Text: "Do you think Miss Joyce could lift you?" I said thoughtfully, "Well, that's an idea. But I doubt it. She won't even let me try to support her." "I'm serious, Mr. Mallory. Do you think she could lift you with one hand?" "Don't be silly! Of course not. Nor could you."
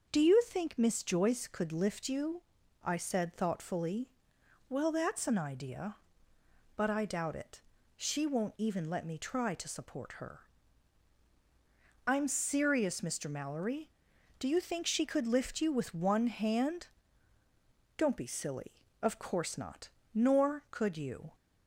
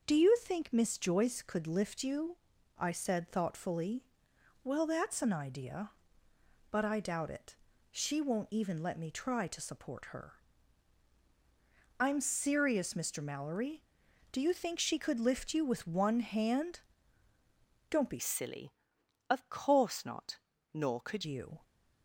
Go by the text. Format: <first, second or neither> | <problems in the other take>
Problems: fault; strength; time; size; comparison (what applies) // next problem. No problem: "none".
first | starts louder than the rest; noticeable; until 1.0 s; 6 dB // changes voice from "silly" to "could"; from 18.1 to 21.2 s; 3.1 s long